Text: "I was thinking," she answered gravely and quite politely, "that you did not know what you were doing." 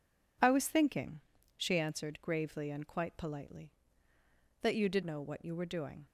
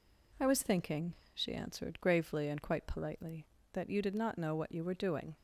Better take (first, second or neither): second